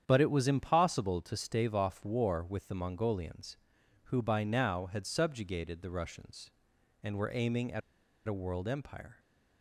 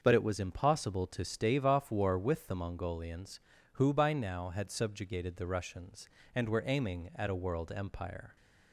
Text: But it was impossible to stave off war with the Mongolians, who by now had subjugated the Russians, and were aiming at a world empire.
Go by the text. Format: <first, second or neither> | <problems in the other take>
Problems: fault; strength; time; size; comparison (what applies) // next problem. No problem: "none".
second | starts louder than the rest; strong; until 1.0 s; 8.5 dB; also in the second // pauses between "at" and "a"; noticeable; at 7.8 s; 0.46 s long